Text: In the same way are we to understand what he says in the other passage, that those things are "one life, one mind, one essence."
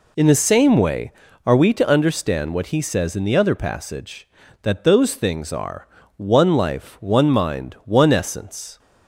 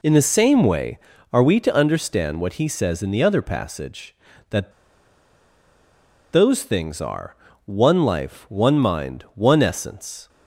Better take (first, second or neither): first